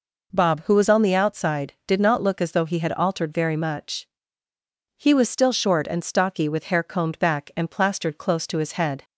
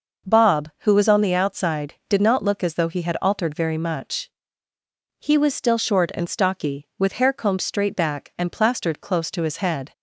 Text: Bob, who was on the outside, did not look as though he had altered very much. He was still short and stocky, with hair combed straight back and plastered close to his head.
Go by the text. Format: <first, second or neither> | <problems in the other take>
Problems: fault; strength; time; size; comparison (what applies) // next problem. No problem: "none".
second | skips "straight"; at 7.1 s